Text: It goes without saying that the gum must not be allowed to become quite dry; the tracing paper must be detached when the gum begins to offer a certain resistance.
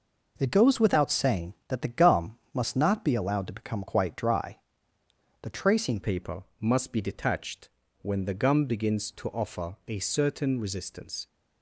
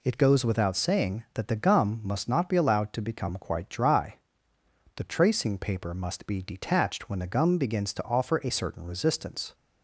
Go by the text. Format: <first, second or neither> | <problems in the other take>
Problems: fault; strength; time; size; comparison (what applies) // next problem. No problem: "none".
second | pauses between "gum" and "must"; slight; at 2.3 s; 0.16 s long // changes voice at "paper"; from 6.0 s on; 5.2 s long // pauses between "paper" and "must"; slight; at 6.4 s; 0.18 s long // pauses between "detached" and "when"; slight; at 7.6 s; 0.34 s long